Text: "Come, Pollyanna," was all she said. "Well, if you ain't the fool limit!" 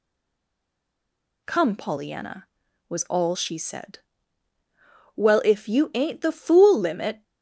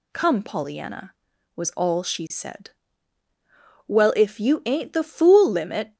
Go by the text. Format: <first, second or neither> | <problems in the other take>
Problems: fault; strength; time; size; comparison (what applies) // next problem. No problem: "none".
second | stays silent before the first word; noticeable; until 1.4 s; 1.4 s long